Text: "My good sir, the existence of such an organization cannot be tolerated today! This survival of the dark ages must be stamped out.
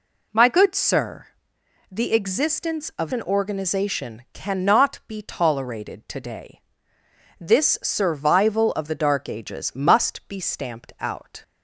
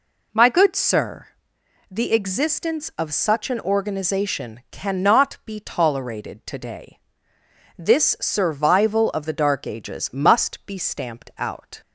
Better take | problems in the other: second | skips "such"; at 3.1 s

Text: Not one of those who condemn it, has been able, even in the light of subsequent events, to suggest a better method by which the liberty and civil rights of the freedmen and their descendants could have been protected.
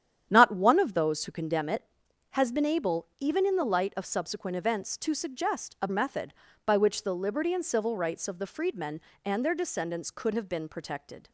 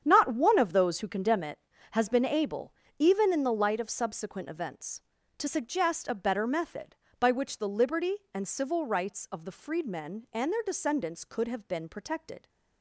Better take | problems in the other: second | starts louder than the rest; strong; until 1.3 s; 9.5 dB; strong in the second // skips "better"; at 5.8 s

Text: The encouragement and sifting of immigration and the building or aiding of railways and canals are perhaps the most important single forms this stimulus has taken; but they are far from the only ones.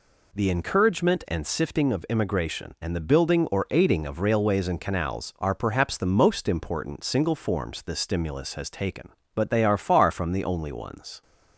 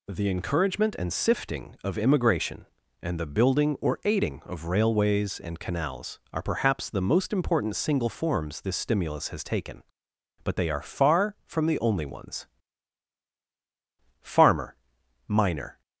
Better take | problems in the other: first | goes on to say "Farmer miner"; from 14.2 s on; 1.5 s long

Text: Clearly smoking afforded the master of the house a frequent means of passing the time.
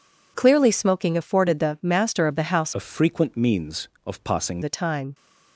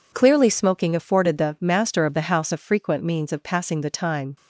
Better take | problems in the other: second | changes voice from "a" to "passing"; from 2.7 to 4.6 s; 1.9 s long

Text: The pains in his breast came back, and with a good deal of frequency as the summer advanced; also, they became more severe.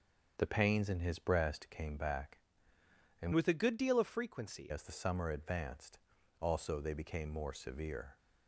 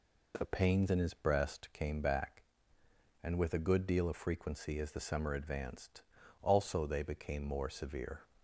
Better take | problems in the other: second | starts louder than the rest; until 1.3 s; 7 dB // changes voice from "with" to "frequency"; from 3.3 to 4.7 s; 1.4 s long

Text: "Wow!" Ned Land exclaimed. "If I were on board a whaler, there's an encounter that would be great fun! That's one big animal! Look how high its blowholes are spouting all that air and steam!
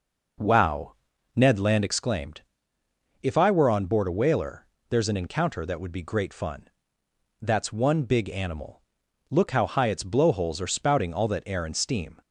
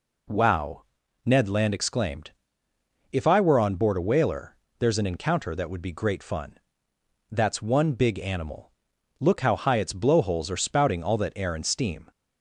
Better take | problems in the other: second | starts louder than the rest; noticeable; until 2.0 s; 5 dB

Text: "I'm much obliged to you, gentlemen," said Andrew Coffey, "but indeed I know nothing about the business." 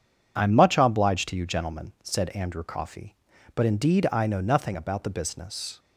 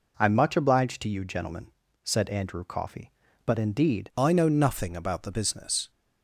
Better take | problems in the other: first | changes voice at "I"; from 4.1 s on; 1.8 s long

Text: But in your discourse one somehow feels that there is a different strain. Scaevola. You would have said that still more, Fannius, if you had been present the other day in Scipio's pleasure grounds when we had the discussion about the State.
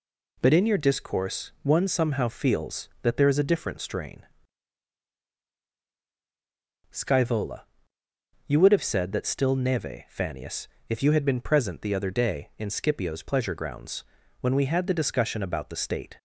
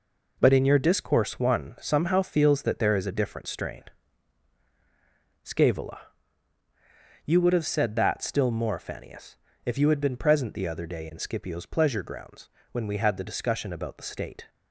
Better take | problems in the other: second | says "neve" for "more"; at 9.5 s // pauses between "grounds" and "when"; slight; at 14.0 s; 0.36 s long; slight in the second

